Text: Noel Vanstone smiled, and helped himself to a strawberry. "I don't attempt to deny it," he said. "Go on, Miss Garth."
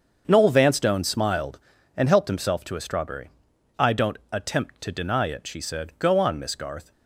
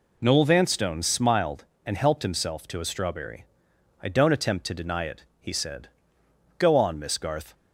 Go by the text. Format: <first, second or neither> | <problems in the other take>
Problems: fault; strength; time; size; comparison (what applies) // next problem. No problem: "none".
second | starts louder than the rest; until 1.2 s; 7 dB // pauses between "don't" and "attempt"; slight; at 4.1 s; 0.16 s long // says "she" for "he"; at 5.4 s